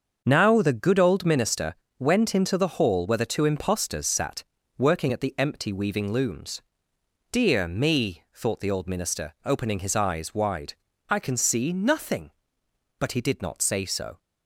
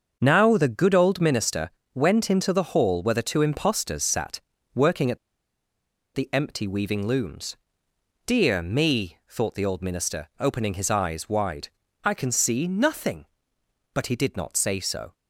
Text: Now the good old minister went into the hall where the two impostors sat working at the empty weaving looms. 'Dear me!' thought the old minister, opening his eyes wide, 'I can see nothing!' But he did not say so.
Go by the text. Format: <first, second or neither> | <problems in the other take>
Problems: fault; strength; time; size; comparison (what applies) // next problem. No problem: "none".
first | starts louder than the rest; until 1.2 s; 7 dB; also in the first // pauses between "minister" and "went"; slight; at 1.7 s; 0.24 s long; slight in the first // pauses between "sat" and "working"; slight; at 4.4 s; 0.34 s long; slight in the first // pauses between "at" and "the"; noticeable; at 5.1 s; 0.96 s long